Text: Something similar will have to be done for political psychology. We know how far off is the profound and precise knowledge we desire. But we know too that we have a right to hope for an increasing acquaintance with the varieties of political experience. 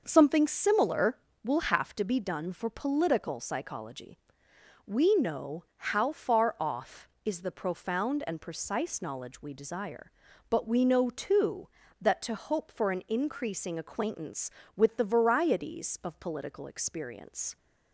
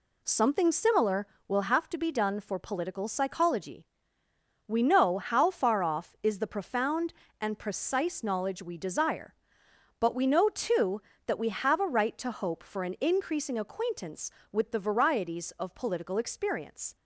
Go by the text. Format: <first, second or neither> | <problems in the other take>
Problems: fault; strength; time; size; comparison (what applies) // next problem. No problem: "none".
second | starts louder than the rest; noticeable; until 1.0 s; 6 dB // skips "we have a right"; at 12.2 s